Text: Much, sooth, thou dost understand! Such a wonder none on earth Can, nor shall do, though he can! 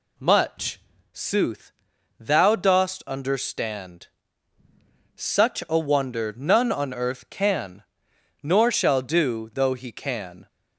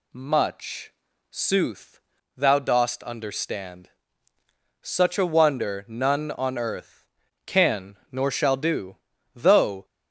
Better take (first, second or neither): first